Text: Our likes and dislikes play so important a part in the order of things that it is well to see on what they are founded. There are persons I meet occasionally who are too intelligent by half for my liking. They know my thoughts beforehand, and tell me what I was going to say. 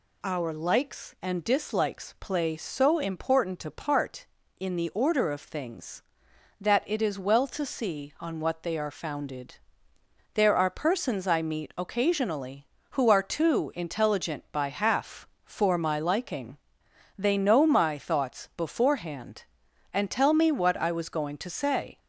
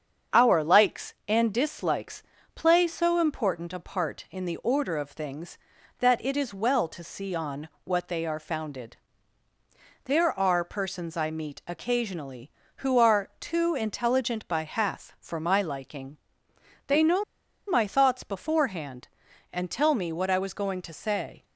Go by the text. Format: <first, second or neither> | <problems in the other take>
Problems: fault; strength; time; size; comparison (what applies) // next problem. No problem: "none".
first | starts louder than the rest; strong; until 1.4 s; 7.5 dB // pauses between "dislikes" and "play"; slight; at 2.2 s; 0.32 s long // pauses between "on" and "what"; slight; at 7.6 s; 0.16 s long // pauses between "know" and "my"; at 17.2 s; 0.44 s long